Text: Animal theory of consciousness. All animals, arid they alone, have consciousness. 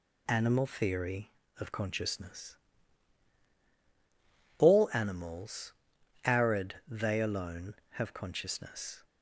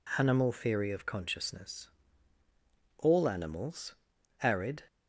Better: first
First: none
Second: stops before "they alone have consciousness"; at 4.8 s

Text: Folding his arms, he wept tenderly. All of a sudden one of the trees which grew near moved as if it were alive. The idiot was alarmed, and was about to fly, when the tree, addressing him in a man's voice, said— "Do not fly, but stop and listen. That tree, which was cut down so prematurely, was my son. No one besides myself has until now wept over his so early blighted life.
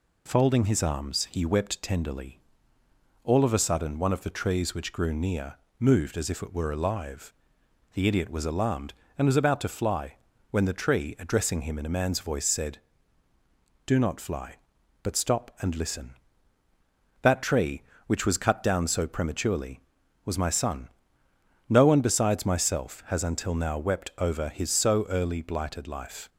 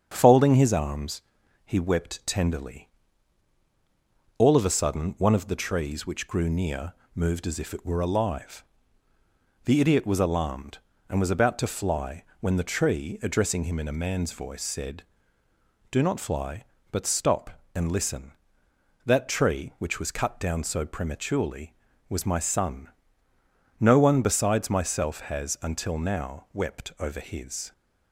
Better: first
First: pauses between "near" and "moved"; slight; at 5.5 s; 0.24 s long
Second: starts louder than the rest; strong; until 1.1 s; 7.5 dB // pauses between "near" and "moved"; slight; at 6.9 s; 0.22 s long // stops before "so early blighted life"; at 27.7 s

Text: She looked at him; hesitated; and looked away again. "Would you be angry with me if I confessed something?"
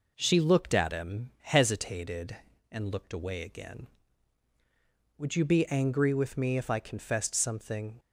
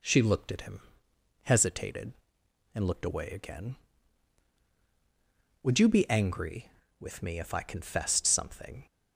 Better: neither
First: none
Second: none

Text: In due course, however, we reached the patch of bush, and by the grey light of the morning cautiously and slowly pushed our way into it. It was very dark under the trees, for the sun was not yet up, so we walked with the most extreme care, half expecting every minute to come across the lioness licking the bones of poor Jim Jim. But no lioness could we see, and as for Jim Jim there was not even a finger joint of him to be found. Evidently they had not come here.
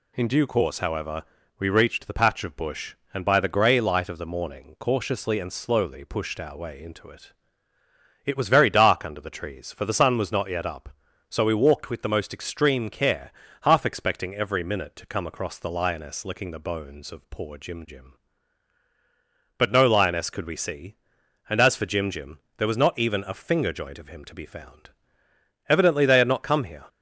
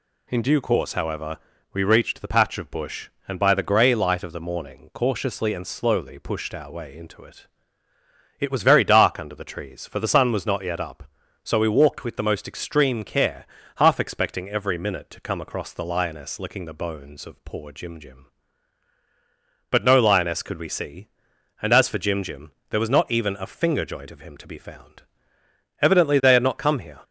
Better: neither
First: pauses between "Jim" and "there"; slight; at 22.3 s; 0.18 s long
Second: pauses between "Jim" and "there"; slight; at 22.5 s; 0.18 s long

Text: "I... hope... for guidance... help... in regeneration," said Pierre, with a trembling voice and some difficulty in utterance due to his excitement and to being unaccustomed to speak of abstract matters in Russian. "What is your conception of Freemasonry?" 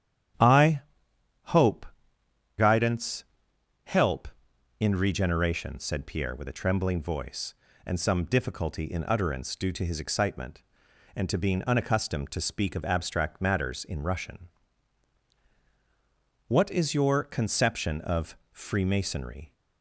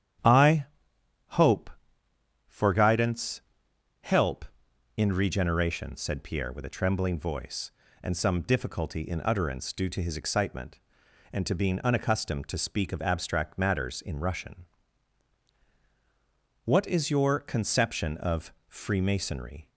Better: second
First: starts louder than the rest; strong; until 2.7 s; 10.5 dB // skips "for"; at 2.2 s // pauses between "of" and "Freemasonry"; slight; at 18.3 s; 0.16 s long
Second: starts louder than the rest; strong; until 2.6 s; 10 dB // pauses between "of" and "Freemasonry"; slight; at 18.5 s; 0.16 s long

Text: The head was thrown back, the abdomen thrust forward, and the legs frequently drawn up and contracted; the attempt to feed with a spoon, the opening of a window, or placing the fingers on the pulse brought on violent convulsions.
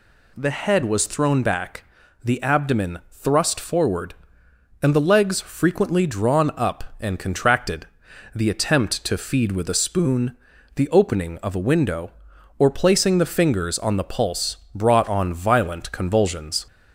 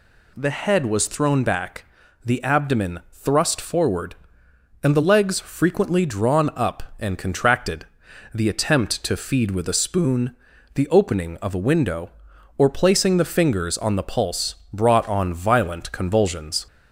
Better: neither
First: none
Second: none

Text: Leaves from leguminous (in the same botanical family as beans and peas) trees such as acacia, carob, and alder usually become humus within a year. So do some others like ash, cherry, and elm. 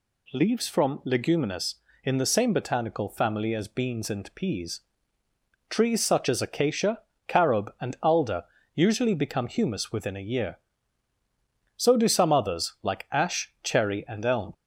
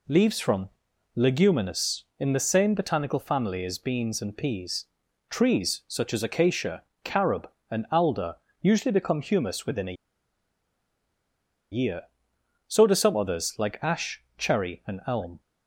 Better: first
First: pauses between "alder" and "usually"; slight; at 8.4 s; 0.32 s long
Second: pauses between "from" and "leguminous"; noticeable; at 0.6 s; 0.46 s long // pauses between "alder" and "usually"; slight; at 8.3 s; 0.24 s long // pauses between "a" and "year"; strong; at 9.9 s; 1.7 s long

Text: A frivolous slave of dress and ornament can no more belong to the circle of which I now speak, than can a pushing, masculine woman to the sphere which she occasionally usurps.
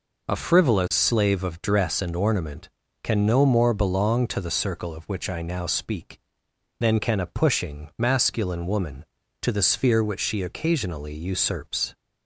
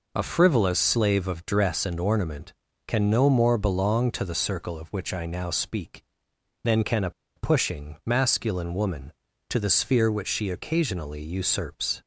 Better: first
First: none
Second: pauses between "a" and "pushing"; slight; at 7.0 s; 0.26 s long

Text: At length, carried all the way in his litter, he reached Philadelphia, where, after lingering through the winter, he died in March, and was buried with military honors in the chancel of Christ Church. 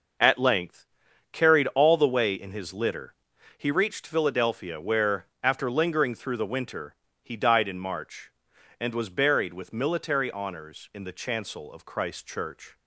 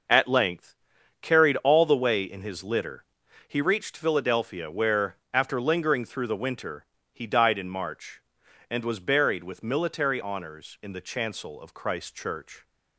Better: neither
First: none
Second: none

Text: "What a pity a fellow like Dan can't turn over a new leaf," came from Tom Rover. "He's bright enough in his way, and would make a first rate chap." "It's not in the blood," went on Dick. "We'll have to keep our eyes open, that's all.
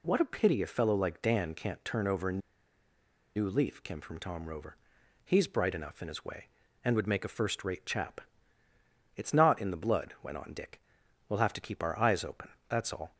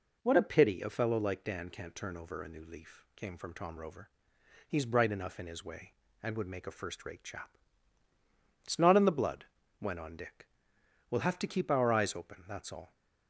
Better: second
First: pauses between "a" and "new"; noticeable; at 2.4 s; 0.95 s long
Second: none

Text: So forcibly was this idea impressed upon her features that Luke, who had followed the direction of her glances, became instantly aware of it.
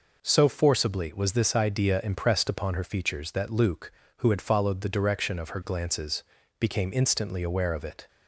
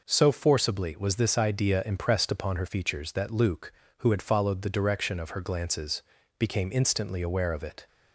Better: neither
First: none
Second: none

